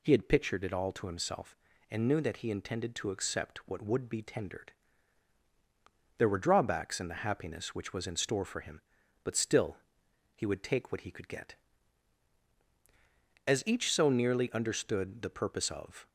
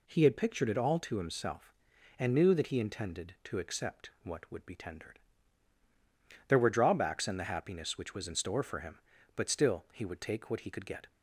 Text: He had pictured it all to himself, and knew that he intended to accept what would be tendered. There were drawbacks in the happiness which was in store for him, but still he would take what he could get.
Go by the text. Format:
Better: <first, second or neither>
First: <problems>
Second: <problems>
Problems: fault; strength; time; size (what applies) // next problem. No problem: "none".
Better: second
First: pauses between "still" and "he"; noticeable; at 9.7 s; 0.58 s long // goes on to say "As each so nearly understood the purpose of"; strong; from 13.4 s on; 2.6 s long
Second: none